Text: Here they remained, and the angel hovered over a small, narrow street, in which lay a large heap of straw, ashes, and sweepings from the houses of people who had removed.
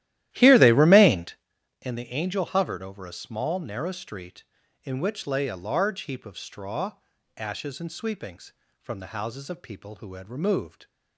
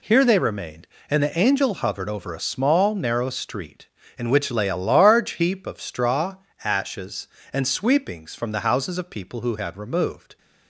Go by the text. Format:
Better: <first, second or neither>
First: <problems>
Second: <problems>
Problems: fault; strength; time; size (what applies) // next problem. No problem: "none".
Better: second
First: starts louder than the rest; strong; until 1.5 s; 14 dB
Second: none